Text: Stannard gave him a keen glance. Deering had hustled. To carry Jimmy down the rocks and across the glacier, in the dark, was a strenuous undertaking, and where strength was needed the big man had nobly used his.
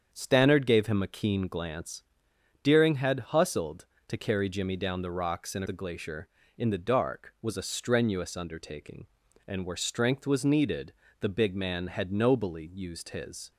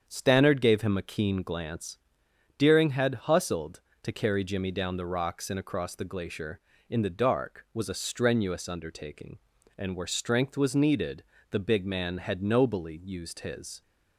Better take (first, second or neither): second